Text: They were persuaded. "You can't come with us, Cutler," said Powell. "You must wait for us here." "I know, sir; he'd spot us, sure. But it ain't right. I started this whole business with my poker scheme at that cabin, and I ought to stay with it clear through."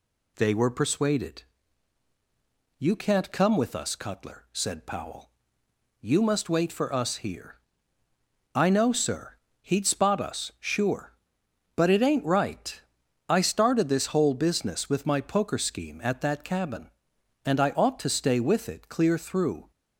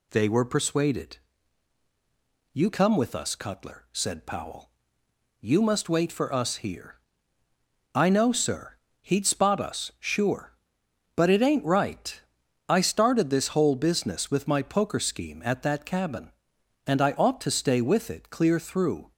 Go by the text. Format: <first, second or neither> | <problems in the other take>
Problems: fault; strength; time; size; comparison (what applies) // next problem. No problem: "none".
first | skips "can't"; at 2.7 s